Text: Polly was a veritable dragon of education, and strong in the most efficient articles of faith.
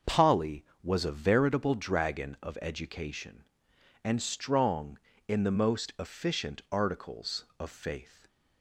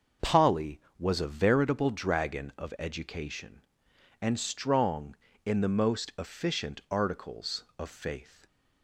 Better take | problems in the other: neither | starts louder than the rest; the same in both

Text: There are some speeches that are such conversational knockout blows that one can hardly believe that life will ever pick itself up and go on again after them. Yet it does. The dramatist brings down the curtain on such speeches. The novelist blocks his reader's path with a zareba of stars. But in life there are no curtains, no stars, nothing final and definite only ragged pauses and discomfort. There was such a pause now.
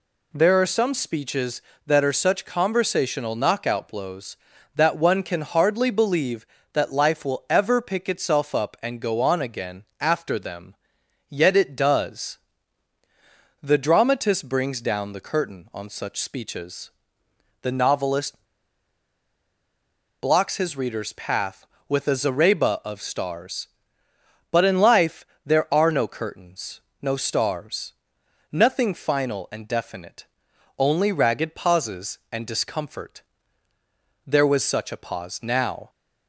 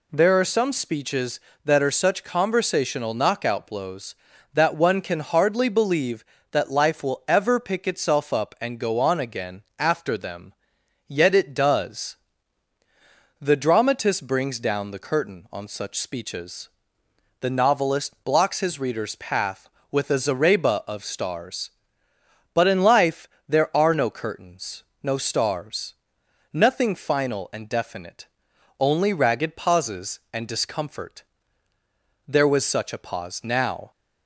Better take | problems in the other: second | pauses between "again" and "after"; slight; at 9.8 s; 0.16 s long; slight in the second // pauses between "novelist" and "blocks"; strong; at 18.3 s; 1.8 s long // pauses between "life" and "there"; slight; at 25.2 s; 0.20 s long; slight in the second // pauses between "definite" and "only"; noticeable; at 30.2 s; 0.56 s long; noticeable in the second

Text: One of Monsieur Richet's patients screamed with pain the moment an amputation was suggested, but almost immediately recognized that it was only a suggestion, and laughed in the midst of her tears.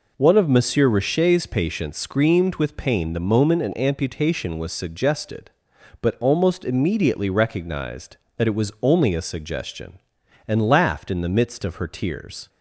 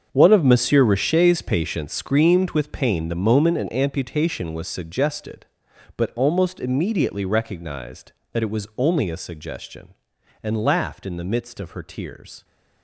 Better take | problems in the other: first | gets quieter; strong; throughout; 13.5 dB

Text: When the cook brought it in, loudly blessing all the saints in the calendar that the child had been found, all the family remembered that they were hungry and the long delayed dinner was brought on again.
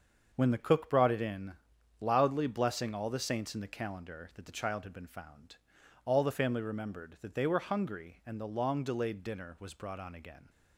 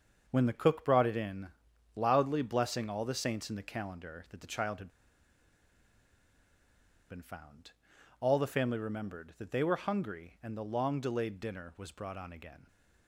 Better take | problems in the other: first | starts louder than the rest; until 1.2 s; 6.5 dB; also in the first // pauses between "had" and "been"; strong; at 4.8 s; 2.2 s long

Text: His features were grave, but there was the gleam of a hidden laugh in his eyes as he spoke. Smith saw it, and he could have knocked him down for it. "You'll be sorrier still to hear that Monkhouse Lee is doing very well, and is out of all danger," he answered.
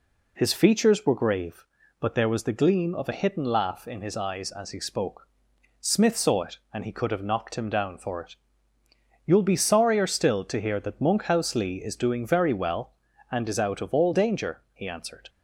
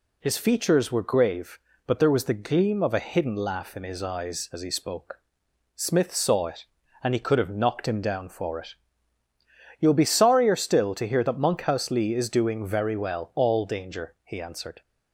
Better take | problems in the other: first | skips "and is out of"; at 13.3 s

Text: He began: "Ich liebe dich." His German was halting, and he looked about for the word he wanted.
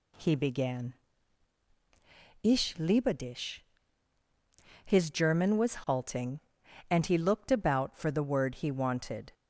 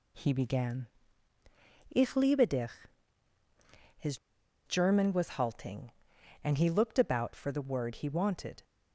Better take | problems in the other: first | pauses between "His" and "German"; noticeable; at 4.1 s; 0.50 s long

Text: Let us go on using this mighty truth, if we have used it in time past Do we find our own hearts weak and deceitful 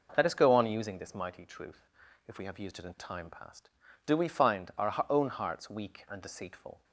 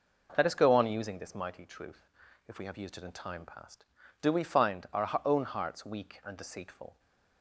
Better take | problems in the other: neither | none

